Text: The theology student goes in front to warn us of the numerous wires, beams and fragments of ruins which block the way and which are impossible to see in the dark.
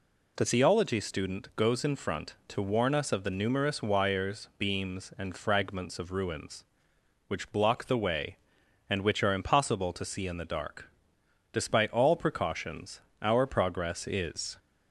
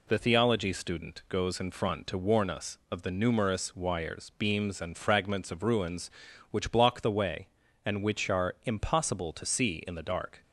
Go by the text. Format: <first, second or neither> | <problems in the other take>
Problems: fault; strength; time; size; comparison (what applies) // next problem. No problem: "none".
second | goes on to say "Despite all precautions our progress is"; strong; from 11.5 s on; 3.0 s long